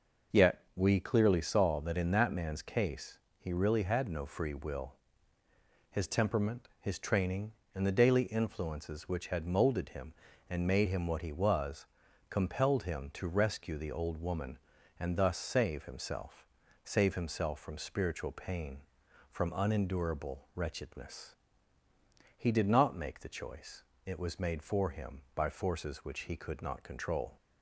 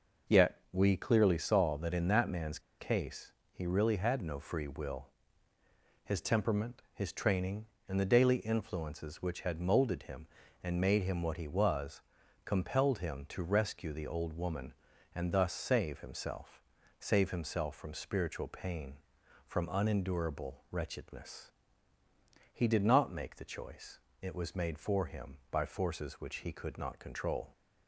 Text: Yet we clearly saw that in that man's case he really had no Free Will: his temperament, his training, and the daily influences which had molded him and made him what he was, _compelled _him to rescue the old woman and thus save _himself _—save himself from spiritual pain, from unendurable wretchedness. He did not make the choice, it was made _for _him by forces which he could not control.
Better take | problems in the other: first | pauses between "man's" and "case"; slight; at 2.5 s; 0.19 s long // pauses between "case" and "he"; slight; at 3.3 s; 0.20 s long; slight in the first

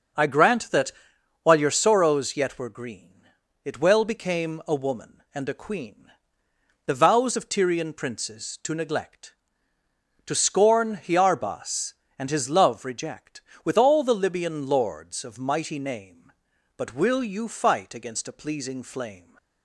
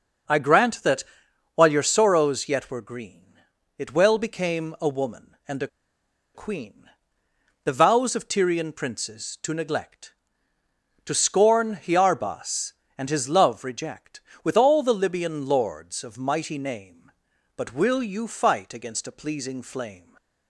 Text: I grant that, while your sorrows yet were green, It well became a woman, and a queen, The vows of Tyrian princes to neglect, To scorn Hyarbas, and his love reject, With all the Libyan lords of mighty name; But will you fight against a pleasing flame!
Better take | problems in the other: first | starts louder than the rest; until 1.7 s; 6 dB; also in the first // pauses between "a" and "queen"; noticeable; at 5.6 s; 0.67 s long

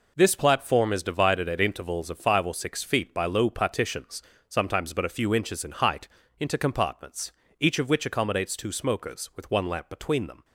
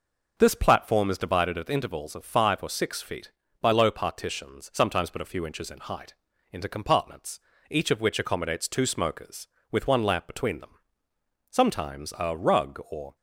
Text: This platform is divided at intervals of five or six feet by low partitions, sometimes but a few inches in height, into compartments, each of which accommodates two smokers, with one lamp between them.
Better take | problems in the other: first | goes on to say "Sometimes a rug or"; from 11.5 s on; 1.6 s long

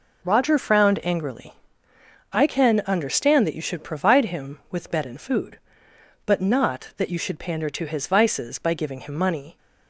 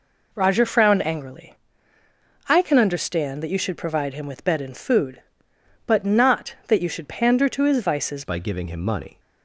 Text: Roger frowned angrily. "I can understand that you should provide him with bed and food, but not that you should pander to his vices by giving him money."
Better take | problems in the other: first | changes voice at "by"; from 8.2 s on; 0.9 s long

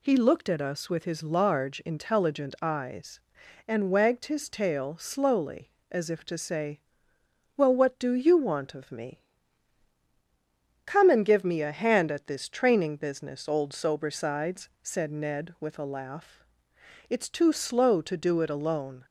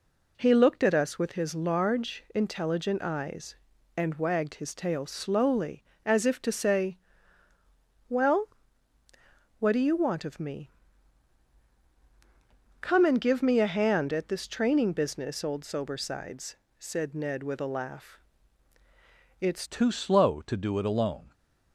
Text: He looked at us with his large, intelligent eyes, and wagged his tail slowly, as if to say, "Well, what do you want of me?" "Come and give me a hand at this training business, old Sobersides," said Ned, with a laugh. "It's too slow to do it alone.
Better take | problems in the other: first | changes voice at "too"; from 19.6 s on; 1.7 s long

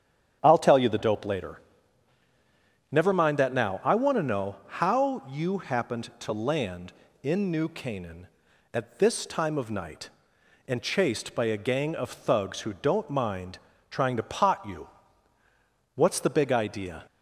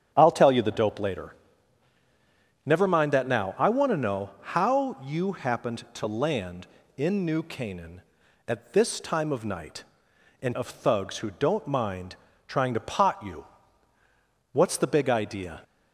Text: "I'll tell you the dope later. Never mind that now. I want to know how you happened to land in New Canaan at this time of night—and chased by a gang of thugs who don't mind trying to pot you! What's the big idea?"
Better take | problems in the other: first | starts louder than the rest; strong; until 1.1 s; 8.5 dB; strong in the first // skips "chased by a gang"; at 10.5 s // pauses between "mind" and "trying"; slight; at 12.1 s; 0.32 s long; slight in the first

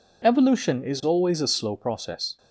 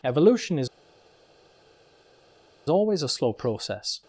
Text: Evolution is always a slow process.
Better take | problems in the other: first | pauses between "is" and "always"; strong; at 0.6 s; 2.0 s long

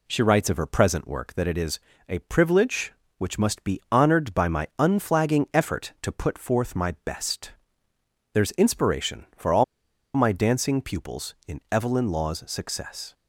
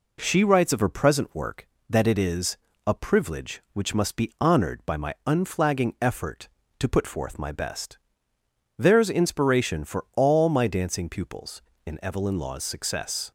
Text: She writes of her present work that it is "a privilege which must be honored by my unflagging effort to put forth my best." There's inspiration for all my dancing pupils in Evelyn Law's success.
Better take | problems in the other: second | pauses between "is" and "a"; slight; at 1.7 s; 0.28 s long; slight in the second // pauses between "all" and "my"; noticeable; at 9.6 s; 0.50 s long

